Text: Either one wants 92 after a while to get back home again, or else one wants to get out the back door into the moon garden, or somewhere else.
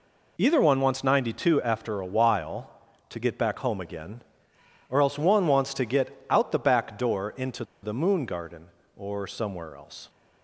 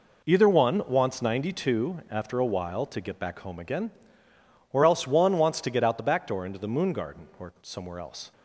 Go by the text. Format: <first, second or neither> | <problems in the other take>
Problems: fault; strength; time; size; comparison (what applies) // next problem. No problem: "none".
second | pauses between "into" and "the"; slight; at 7.6 s; 0.18 s long